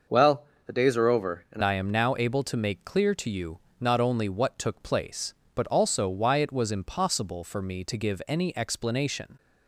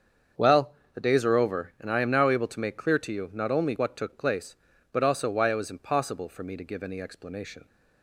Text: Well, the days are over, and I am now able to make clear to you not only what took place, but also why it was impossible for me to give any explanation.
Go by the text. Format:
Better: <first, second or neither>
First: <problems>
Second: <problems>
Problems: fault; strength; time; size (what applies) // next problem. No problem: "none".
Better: second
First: starts louder than the rest; noticeable; until 1.3 s; 6 dB // changes voice at "I"; from 1.6 s on; 7.7 s long // pauses between "you" and "not"; slight; at 3.5 s; 0.22 s long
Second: starts louder than the rest; until 1.5 s; 7 dB